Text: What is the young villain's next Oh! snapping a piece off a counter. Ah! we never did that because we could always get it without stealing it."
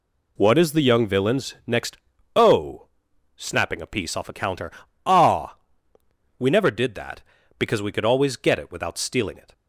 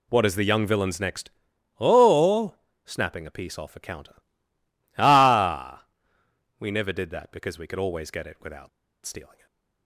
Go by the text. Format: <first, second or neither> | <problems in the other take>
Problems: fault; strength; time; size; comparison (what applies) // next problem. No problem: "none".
first | pauses between "next" and "Oh"; noticeable; at 1.2 s; 0.50 s long; also in the first // pauses between "without" and "stealing"; at 8.6 s; 0.36 s long // stays silent after the last word; slight; from 9.2 s on; 0.6 s long